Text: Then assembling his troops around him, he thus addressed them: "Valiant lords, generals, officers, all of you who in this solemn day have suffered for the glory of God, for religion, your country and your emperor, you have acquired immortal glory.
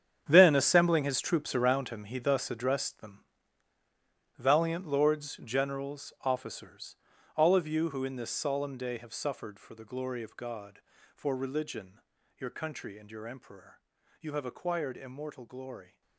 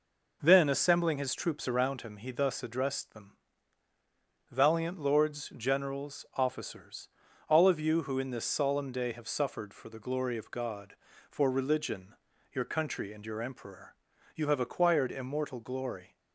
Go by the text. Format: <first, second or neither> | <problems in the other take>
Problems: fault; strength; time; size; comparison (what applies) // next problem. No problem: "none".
second | gets quieter; strong; throughout; 14 dB